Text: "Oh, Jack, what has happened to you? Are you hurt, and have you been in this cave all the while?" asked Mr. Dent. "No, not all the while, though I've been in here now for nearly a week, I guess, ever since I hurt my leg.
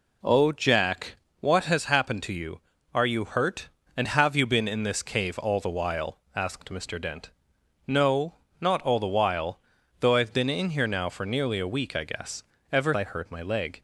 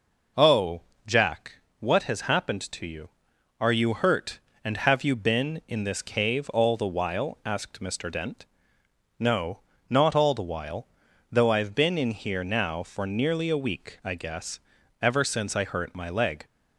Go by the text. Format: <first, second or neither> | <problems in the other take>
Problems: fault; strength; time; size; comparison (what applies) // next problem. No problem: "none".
second | skips "since"; at 12.9 s